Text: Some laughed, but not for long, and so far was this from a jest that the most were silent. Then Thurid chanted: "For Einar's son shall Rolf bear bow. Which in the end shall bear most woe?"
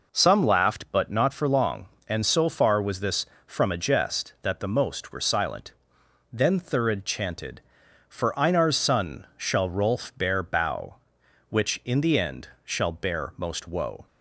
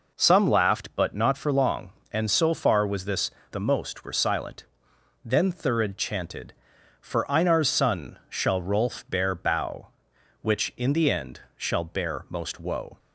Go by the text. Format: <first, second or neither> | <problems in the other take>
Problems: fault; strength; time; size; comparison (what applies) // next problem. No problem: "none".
first | skips "from a jest that"; at 3.4 s // pauses between "end" and "shall"; slight; at 11.3 s; 0.18 s long; slight in the first